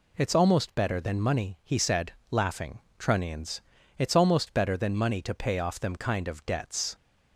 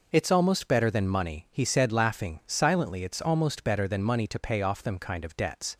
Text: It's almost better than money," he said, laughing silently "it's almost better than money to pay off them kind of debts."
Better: second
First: says "trunnions" for "silently"; at 2.9 s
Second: none

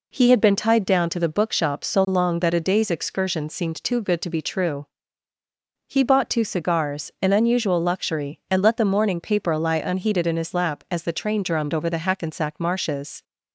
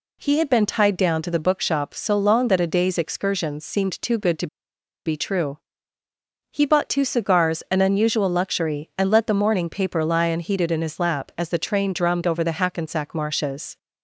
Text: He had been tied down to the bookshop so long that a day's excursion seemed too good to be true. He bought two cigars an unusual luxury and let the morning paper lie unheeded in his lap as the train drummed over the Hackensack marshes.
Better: first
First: none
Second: pauses between "to" and "be"; noticeable; at 4.4 s; 0.59 s long

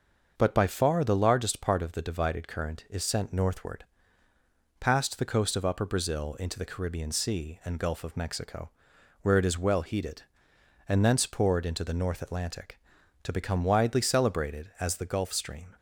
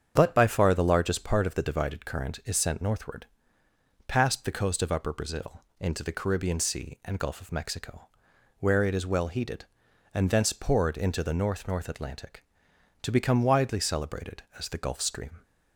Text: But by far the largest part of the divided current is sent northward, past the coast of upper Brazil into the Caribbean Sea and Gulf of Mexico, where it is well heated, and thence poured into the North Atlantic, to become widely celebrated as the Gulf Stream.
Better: first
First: starts louder than the rest; until 1.3 s; 6.5 dB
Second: starts louder than the rest; strong; until 1.1 s; 8 dB // pauses between "Brazil" and "into"; slight; at 5.6 s; 0.18 s long // says "North" twice; at 11.6 s

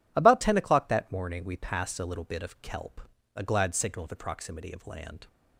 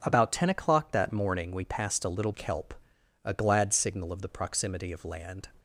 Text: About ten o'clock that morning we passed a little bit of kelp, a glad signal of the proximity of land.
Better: first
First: none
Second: skips "bit of"; at 2.3 s

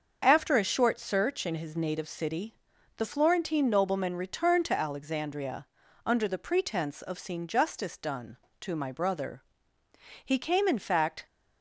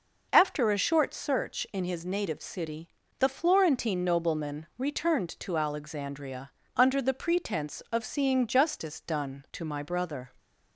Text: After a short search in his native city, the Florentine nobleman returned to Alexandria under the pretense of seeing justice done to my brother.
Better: second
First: starts louder than the rest; until 1.2 s; 6.5 dB // pauses between "Alexandria" and "under"; at 5.6 s; 0.40 s long // goes on to say "He came in fact"; noticeable; from 10.2 s on; 1.0 s long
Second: pauses between "Alexandria" and "under"; slight; at 6.5 s; 0.26 s long

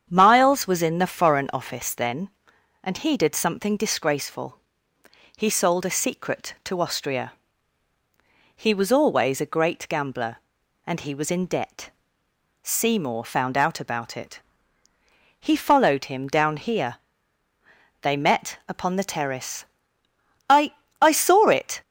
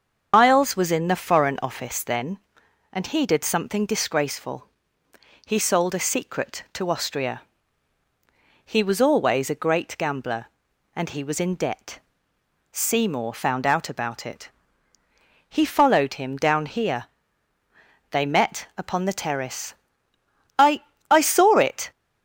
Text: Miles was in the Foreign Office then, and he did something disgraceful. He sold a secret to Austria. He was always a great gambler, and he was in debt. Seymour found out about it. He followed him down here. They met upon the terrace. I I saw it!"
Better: first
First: starts louder than the rest; strong; until 1.1 s; 8 dB // pauses between "I" and "I"; slight; at 20.7 s; 0.30 s long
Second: loses the start of "Miles"; at 0.3 s; 150 ms // starts louder than the rest; until 1.3 s; 7 dB // pauses between "I" and "I"; slight; at 20.8 s; 0.30 s long

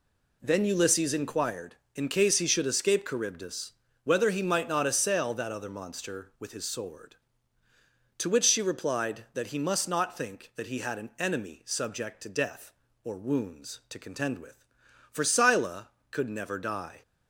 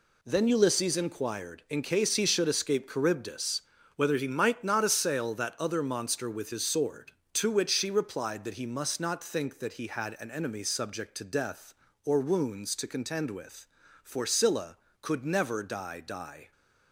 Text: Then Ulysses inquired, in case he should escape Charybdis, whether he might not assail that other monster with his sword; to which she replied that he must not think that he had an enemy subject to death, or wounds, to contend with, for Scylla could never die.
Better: first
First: none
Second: says "die" twice; at 16.0 s

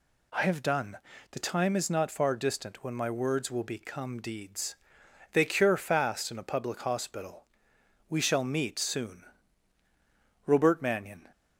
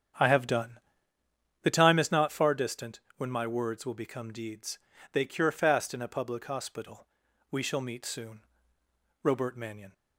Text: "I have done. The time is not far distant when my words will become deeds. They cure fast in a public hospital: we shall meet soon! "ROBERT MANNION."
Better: first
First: none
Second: starts louder than the rest; strong; until 1.2 s; 8.5 dB // pauses between "distant" and "when"; slight; at 3.0 s; 0.16 s long

